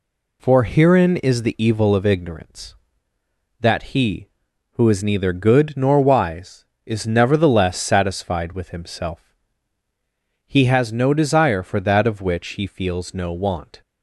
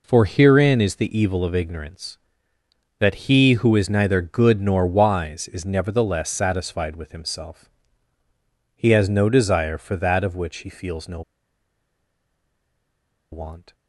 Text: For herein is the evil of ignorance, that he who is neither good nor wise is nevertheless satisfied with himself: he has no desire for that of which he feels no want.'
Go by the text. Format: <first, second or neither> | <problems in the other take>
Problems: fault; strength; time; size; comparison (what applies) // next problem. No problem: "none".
first | pauses between "no" and "want"; strong; at 11.2 s; 2.1 s long